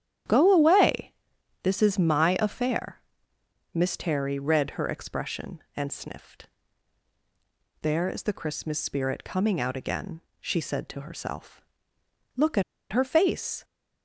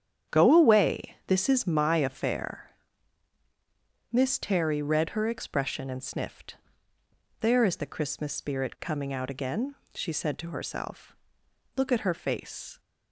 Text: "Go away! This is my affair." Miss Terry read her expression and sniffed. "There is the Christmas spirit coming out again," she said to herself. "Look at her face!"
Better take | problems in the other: second | starts louder than the rest; strong; until 1.7 s; 10 dB; strong in the second // pauses between "at" and "her"; slight; at 12.6 s; 0.28 s long

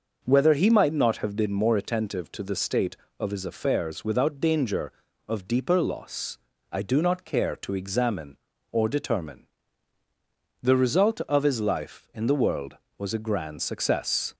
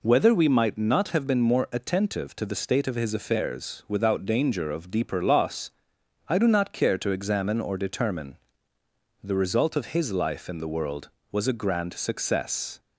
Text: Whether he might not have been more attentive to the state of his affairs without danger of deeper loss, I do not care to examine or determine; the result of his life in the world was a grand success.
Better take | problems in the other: first | says "we" for "he"; at 0.3 s

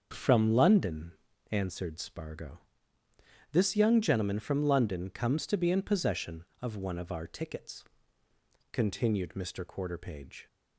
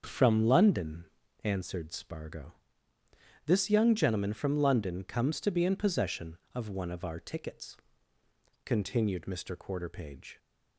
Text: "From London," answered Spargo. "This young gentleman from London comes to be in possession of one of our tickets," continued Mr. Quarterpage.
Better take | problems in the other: neither | starts louder than the rest; the same in both

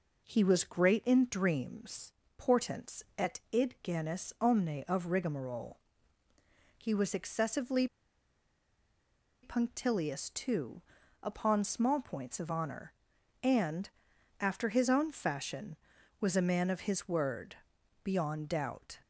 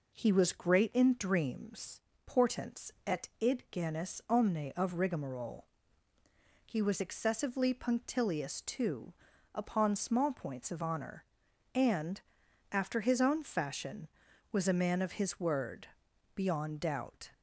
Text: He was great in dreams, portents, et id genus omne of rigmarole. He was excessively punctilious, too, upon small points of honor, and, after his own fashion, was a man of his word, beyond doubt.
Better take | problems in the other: second | pauses between "excessively" and "punctilious"; strong; at 7.8 s; 1.5 s long

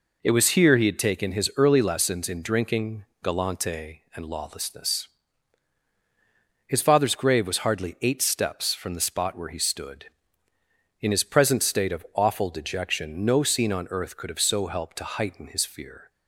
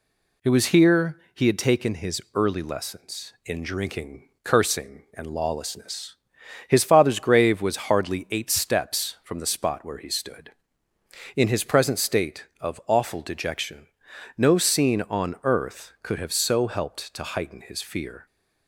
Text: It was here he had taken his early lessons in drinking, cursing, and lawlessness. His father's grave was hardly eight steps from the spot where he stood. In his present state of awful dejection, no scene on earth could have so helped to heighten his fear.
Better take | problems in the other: second | says "galante" for "cursing"; at 3.2 s

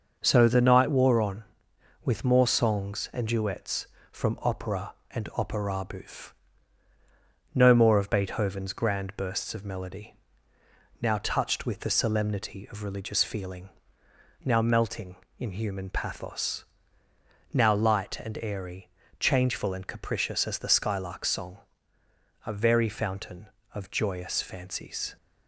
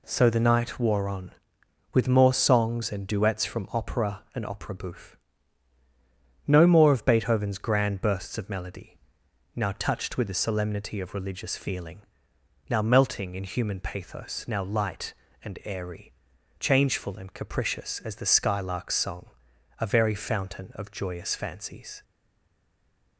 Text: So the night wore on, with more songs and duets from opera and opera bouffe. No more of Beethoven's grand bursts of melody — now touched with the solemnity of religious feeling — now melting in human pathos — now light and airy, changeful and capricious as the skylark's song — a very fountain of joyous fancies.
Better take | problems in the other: first | stays silent after the last word; noticeable; from 22.0 s on; 1.1 s long

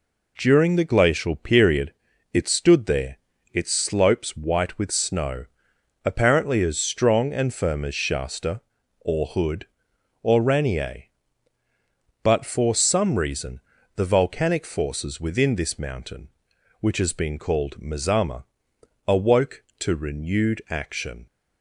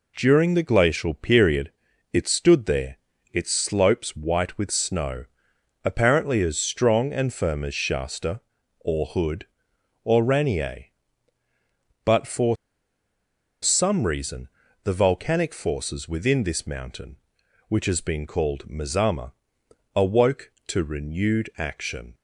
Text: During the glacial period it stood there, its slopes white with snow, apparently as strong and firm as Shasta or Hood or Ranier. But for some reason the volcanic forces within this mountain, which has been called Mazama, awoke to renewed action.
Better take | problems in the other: first | pauses between "period" and "it"; at 1.7 s; 0.40 s long; also in the first // pauses between "for" and "some"; at 12.5 s; 1.0 s long // pauses between "reason" and "the"; slight; at 14.4 s; 0.36 s long; slight in the first

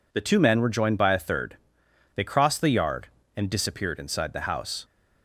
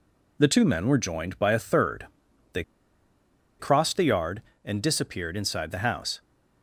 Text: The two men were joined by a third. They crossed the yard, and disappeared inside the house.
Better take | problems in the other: first | pauses between "They" and "crossed"; noticeable; at 2.6 s; 0.97 s long

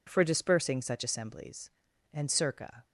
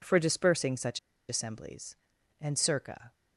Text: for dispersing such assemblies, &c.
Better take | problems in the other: first | pauses between "such" and "assemblies"; slight; at 0.9 s; 0.30 s long

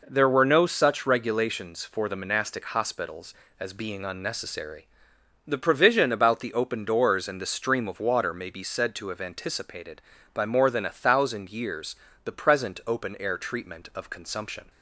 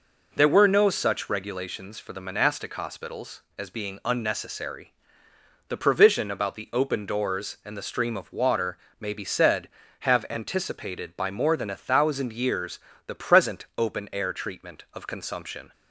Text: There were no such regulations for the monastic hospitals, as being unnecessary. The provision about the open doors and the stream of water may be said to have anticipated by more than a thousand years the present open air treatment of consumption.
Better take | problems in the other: first | pauses between "water" and "may"; slight; at 8.7 s; 0.20 s long // skips "to"; at 9.8 s // pauses between "years" and "the"; slight; at 12.7 s; 0.28 s long; slight in the first

